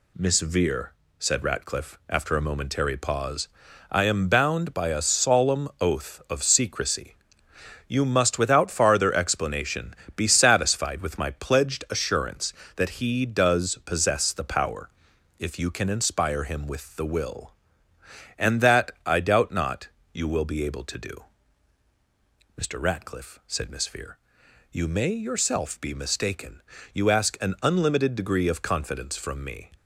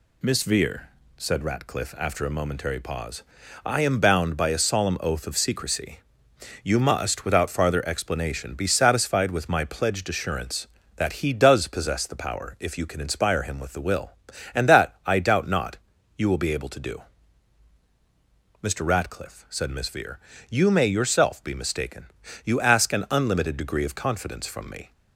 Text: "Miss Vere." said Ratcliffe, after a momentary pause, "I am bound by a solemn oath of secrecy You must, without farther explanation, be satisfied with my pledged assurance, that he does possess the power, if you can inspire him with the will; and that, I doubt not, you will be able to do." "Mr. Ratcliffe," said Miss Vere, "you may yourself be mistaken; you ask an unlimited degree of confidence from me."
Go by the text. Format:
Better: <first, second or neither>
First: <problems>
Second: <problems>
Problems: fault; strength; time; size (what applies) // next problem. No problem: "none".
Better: neither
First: pauses between "secrecy" and "You"; noticeable; at 7.1 s; 0.72 s long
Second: pauses between "secrecy" and "You"; noticeable; at 5.9 s; 0.66 s long